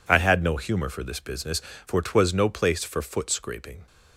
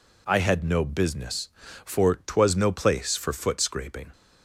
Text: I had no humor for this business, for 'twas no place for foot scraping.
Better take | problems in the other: first | skips "humor for this"; at 0.8 s

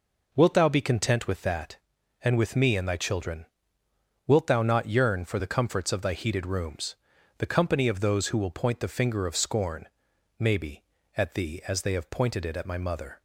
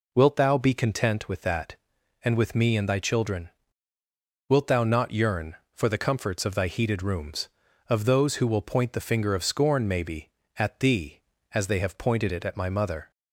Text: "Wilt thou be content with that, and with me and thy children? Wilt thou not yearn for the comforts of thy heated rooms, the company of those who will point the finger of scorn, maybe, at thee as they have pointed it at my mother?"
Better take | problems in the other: first | skips "the company"; at 7.6 s

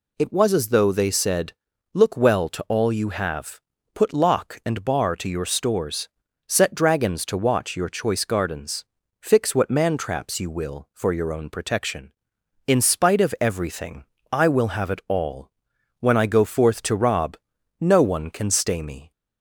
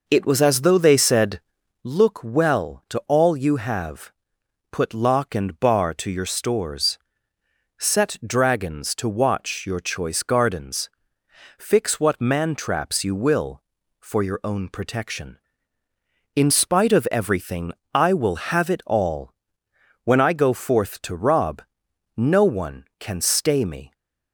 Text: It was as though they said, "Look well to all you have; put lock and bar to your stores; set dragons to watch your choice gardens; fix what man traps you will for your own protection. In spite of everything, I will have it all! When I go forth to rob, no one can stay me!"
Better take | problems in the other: first | starts louder than the rest; noticeable; until 2.0 s; 5 dB

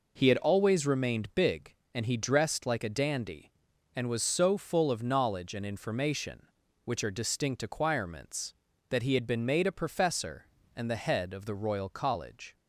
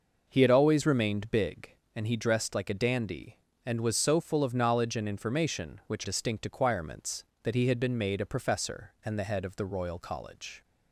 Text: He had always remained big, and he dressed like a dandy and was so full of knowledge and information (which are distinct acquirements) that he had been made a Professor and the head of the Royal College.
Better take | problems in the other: first | skips "are"; at 6.0 s

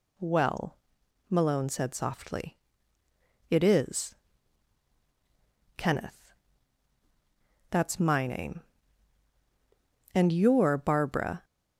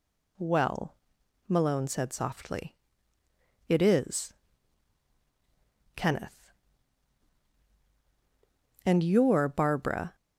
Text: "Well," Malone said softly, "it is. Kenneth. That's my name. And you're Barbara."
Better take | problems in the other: first | skips "That's my name"; at 7.6 s

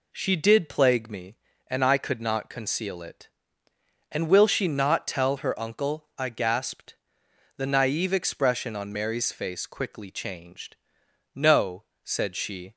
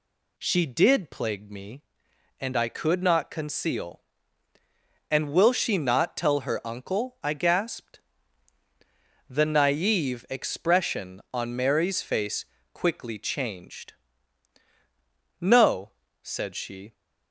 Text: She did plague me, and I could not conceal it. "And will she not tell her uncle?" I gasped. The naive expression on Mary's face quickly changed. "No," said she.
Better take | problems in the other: first | skips "it"; at 4.5 s // pauses between "face" and "quickly"; slight; at 12.4 s; 0.30 s long

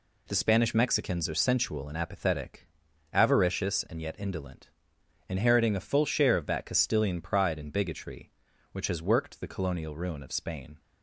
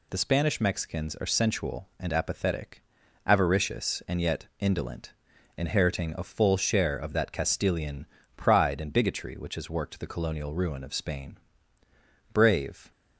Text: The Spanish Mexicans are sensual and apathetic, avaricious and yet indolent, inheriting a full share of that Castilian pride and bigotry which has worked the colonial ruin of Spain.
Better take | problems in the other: first | pauses between "Castilian" and "pride"; slight; at 8.0 s; 0.28 s long // goes on to say "Brave"; from 12.3 s on; 0.58 s long

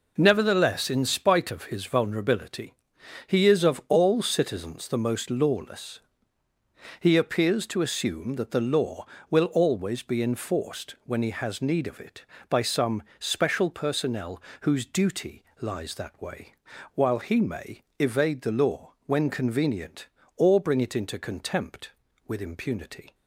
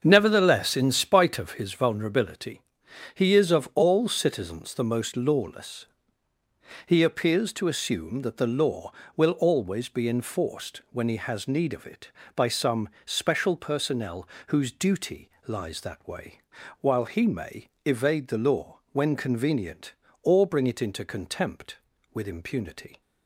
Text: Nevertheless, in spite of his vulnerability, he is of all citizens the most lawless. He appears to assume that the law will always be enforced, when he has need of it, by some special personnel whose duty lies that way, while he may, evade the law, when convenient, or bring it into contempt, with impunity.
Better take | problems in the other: first | starts louder than the rest; until 1.7 s; 7 dB // pauses between "some" and "special"; slight; at 12.8 s; 0.16 s long; slight in the first // pauses between "personnel" and "whose"; slight; at 14.2 s; 0.20 s long; slight in the first // pauses between "duty" and "lies"; slight; at 15.3 s; 0.18 s long; slight in the first

